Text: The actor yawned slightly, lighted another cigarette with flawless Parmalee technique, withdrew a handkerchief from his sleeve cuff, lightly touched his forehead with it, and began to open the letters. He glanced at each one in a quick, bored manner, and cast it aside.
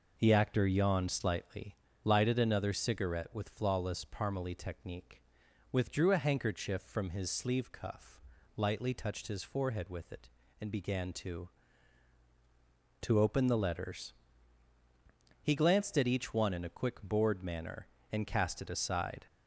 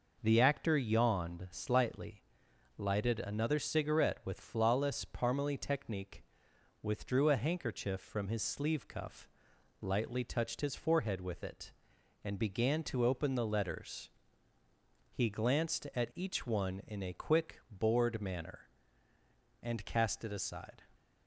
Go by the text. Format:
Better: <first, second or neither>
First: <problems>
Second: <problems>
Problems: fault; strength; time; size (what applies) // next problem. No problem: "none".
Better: second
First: says "to" twice; at 13.0 s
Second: none